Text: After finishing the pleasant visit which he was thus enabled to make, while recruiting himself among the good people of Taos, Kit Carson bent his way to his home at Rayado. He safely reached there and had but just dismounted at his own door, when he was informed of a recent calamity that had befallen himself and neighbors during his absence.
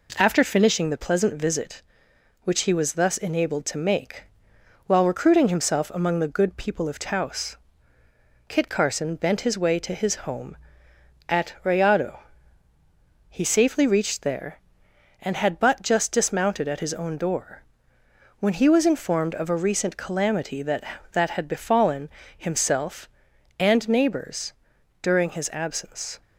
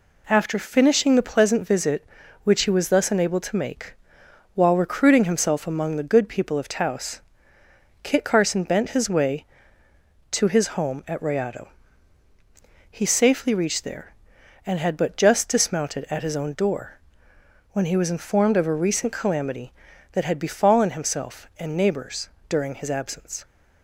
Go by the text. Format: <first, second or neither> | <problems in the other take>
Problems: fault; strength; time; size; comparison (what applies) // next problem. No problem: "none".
second | says "that" twice; at 21.1 s // pauses between "befallen" and "himself"; slight; at 22.0 s; 0.28 s long // pauses between "neighbors" and "during"; noticeable; at 24.5 s; 0.50 s long; slight in the second